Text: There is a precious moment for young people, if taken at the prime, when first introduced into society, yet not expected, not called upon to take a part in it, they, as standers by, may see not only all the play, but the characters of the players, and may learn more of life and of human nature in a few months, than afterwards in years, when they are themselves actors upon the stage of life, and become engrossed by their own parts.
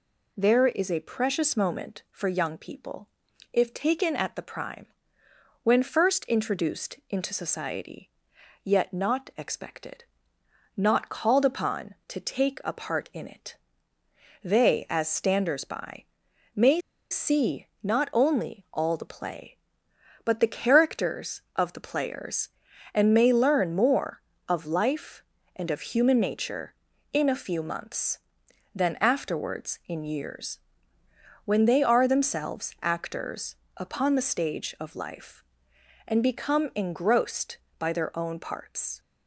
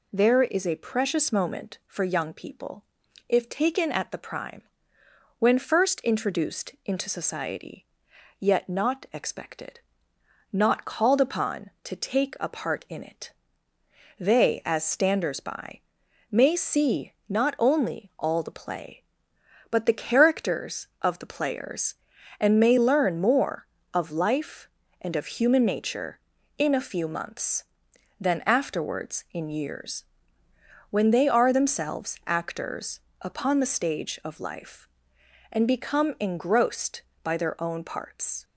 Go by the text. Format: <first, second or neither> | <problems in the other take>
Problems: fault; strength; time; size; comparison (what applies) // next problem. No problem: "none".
second | pauses between "may" and "see"; slight; at 16.7 s; 0.31 s long // pauses between "see" and "not"; slight; at 17.6 s; 0.16 s long; slight in the second // pauses between "actors" and "upon"; slight; at 33.5 s; 0.20 s long; slight in the second